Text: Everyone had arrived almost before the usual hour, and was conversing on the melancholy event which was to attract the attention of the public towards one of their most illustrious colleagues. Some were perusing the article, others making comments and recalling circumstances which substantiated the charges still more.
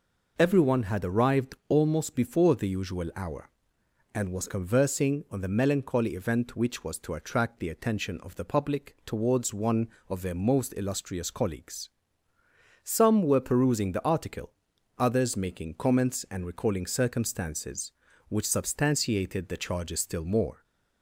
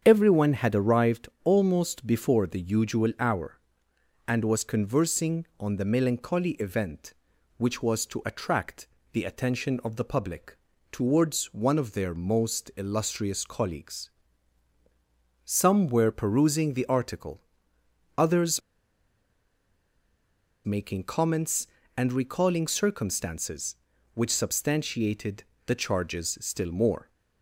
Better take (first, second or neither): first